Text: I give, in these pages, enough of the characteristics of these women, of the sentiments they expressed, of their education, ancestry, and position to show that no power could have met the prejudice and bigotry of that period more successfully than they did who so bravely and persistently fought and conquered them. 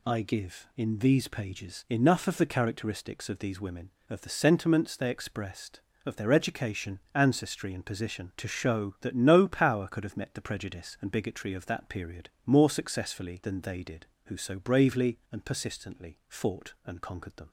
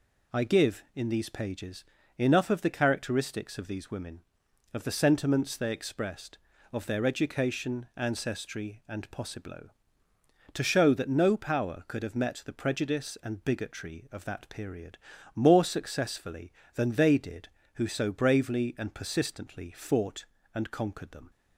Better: first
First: pauses between "period" and "more"; slight; at 12.2 s; 0.16 s long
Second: says "possiblo" for "position"; at 9.0 s // pauses between "period" and "more"; at 14.9 s; 0.40 s long

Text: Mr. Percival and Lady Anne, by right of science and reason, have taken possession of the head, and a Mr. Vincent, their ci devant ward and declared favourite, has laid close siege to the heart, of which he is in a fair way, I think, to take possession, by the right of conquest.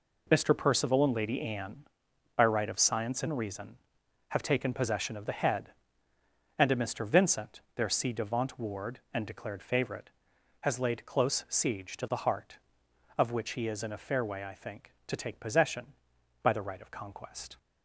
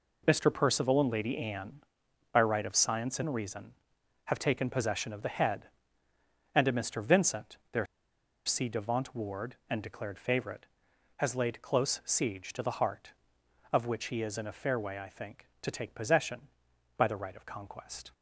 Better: first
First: none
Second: pauses between "their" and "ci"; noticeable; at 7.8 s; 0.61 s long

